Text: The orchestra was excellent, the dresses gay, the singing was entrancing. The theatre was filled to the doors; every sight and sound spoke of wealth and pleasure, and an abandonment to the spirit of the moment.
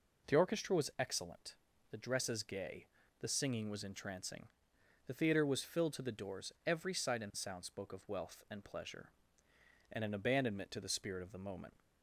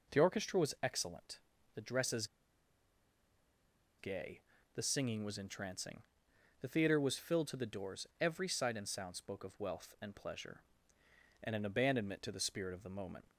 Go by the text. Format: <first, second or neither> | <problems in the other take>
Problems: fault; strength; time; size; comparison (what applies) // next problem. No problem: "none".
first | pauses between "dresses" and "gay"; strong; at 2.2 s; 1.7 s long